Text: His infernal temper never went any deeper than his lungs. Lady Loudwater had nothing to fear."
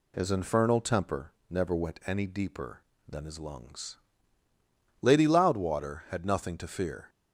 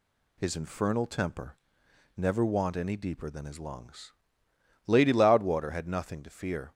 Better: first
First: pauses between "temper" and "never"; slight; at 1.3 s; 0.16 s long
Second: pauses between "temper" and "never"; noticeable; at 1.5 s; 0.58 s long // says "want" for "went"; at 2.4 s

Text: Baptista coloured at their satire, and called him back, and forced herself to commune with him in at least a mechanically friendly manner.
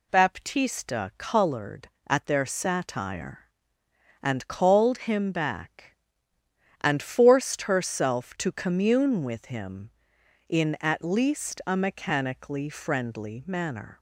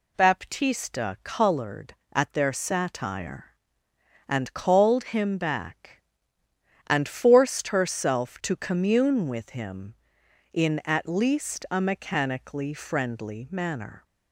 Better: neither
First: none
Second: none

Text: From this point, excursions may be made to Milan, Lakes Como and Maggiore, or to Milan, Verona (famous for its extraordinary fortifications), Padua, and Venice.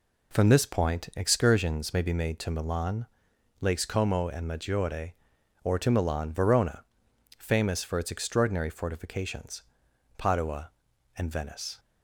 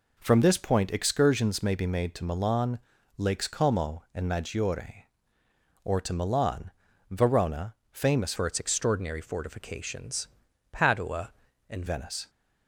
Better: first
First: none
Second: changes voice from "for" to "and"; from 8.3 to 11.8 s; 3.5 s long

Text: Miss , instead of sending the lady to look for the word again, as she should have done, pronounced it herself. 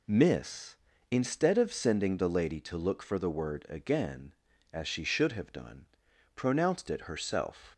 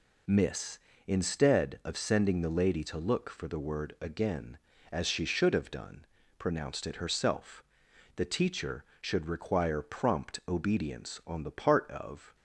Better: first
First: none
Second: goes on to say "The teacher should require prompt obedience on the part of"; strong; from 8.1 s on; 4.2 s long

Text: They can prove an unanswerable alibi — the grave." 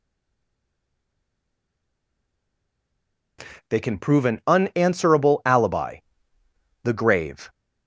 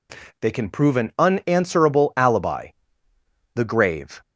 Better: second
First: stays silent before the first word; strong; until 3.3 s; 3.3 s long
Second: none

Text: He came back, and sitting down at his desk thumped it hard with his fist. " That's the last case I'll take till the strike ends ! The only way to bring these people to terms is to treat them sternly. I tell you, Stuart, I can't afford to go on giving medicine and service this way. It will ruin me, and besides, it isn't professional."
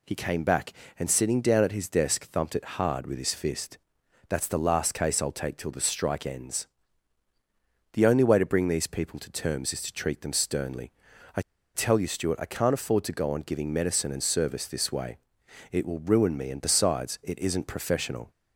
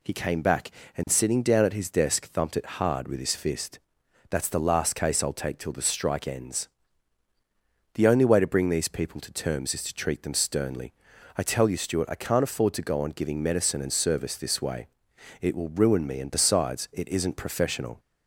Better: second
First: pauses between "I" and "tell"; slight; at 11.4 s; 0.34 s long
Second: none

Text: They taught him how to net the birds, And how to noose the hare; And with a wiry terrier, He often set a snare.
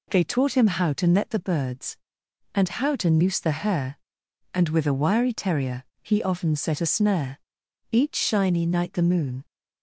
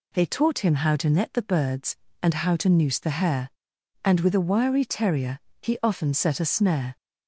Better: second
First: goes on to say "Each shiny night the moon"; from 7.9 s on; 1.5 s long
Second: none

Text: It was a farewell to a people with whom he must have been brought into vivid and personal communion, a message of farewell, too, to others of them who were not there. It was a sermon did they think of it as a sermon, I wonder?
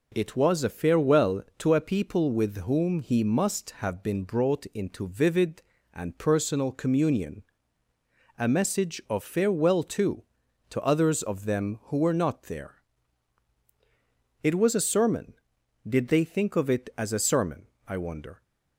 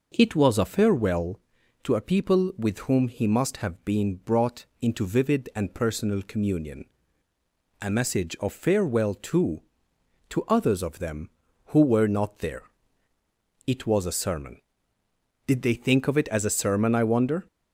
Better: neither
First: none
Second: none

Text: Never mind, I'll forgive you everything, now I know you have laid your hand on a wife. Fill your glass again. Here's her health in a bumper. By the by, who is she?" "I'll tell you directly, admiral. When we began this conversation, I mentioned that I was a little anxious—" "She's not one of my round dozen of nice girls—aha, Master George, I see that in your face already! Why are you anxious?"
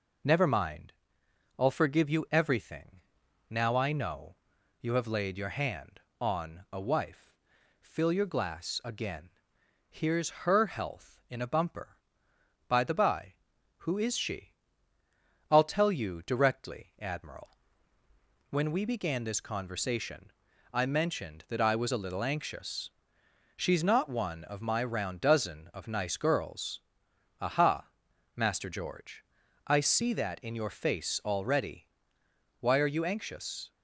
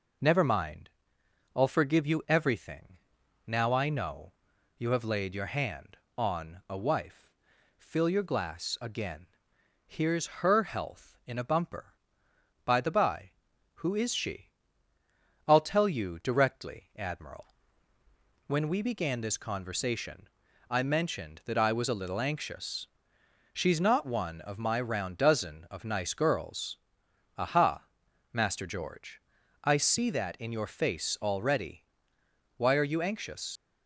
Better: first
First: pauses between "know" and "you"; at 4.3 s; 0.44 s long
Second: pauses between "know" and "you"; at 4.3 s; 0.44 s long // leaves "anxious" unfinished; at 33.5 s; 130 ms

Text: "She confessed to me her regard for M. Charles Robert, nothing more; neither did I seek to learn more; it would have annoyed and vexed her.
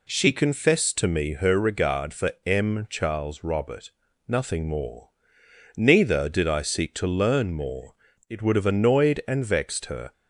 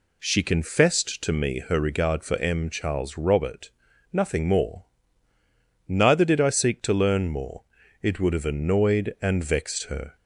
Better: neither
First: none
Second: none

